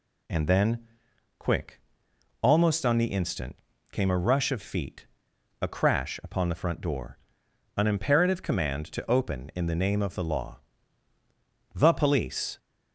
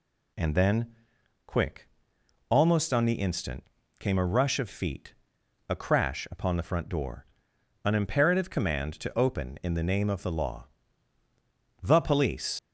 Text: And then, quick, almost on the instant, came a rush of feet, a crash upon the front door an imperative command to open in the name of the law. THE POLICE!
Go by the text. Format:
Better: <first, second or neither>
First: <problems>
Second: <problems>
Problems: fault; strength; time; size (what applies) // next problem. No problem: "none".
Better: first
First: pauses between "door" and "an"; noticeable; at 7.1 s; 0.60 s long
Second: pauses between "door" and "an"; noticeable; at 7.2 s; 0.60 s long // leaves "POLICE" unfinished; at 12.5 s; 65 ms